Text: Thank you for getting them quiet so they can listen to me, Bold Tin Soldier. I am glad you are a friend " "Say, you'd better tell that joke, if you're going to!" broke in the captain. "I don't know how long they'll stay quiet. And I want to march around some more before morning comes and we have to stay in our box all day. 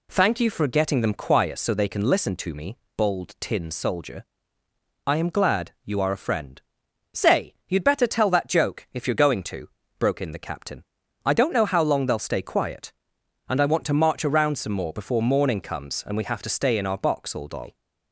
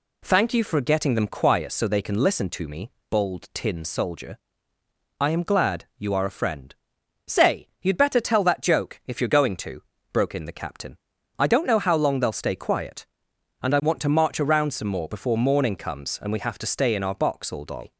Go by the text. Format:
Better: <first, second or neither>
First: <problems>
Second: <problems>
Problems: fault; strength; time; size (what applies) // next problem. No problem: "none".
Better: neither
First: none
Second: none